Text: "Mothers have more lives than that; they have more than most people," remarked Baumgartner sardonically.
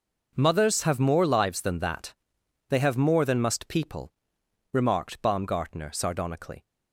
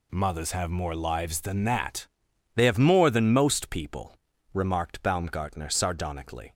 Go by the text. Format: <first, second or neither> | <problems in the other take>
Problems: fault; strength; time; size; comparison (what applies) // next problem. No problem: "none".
second | says "must" for "most"; at 3.3 s